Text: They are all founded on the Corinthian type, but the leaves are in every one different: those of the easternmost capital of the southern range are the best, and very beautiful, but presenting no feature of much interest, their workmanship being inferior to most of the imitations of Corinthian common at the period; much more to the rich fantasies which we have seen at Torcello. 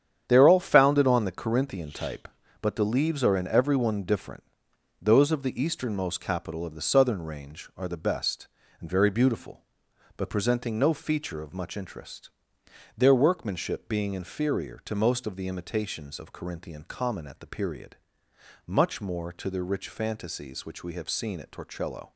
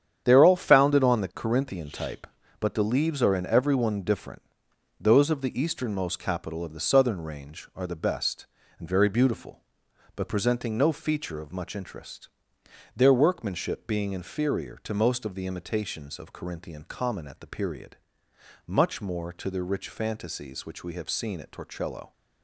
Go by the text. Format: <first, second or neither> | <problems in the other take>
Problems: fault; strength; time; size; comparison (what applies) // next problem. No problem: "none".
neither | starts louder than the rest; strong; the same in both